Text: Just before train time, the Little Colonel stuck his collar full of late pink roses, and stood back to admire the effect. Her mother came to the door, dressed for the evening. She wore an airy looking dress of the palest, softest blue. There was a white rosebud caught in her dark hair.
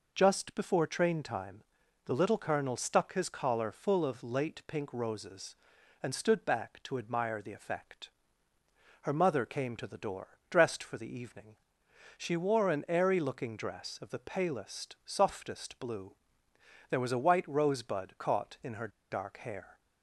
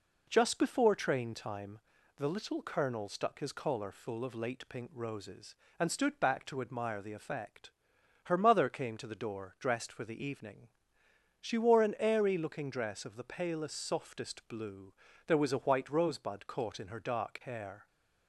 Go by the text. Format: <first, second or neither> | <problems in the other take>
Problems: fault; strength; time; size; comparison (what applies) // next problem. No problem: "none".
second | pauses between "her" and "dark"; slight; at 18.8 s; 0.22 s long